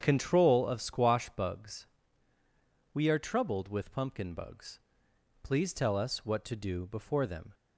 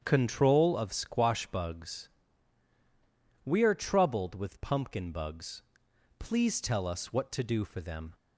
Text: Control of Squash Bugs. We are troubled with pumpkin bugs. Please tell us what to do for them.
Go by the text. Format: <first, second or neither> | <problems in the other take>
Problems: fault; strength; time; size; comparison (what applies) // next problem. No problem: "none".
second | starts louder than the rest; strong; until 1.0 s; 8 dB; strong in the second // says "before" for "for"; at 6.8 s